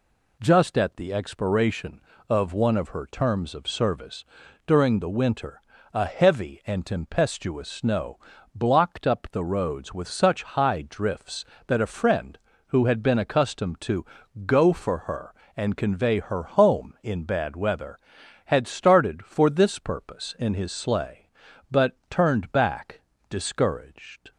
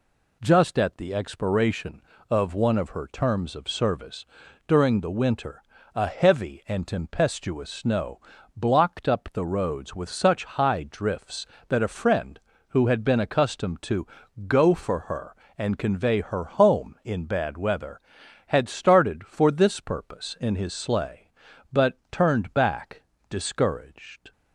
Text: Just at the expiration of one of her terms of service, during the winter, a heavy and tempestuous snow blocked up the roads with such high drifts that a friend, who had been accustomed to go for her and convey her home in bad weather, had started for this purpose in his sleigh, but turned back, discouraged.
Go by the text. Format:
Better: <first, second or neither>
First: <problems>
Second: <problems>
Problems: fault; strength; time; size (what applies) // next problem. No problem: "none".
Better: neither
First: pauses between "snow" and "blocked"; slight; at 8.1 s; 0.34 s long // pauses between "to" and "go"; at 14.0 s; 0.40 s long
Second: pauses between "snow" and "blocked"; slight; at 8.2 s; 0.34 s long // pauses between "to" and "go"; at 14.0 s; 0.40 s long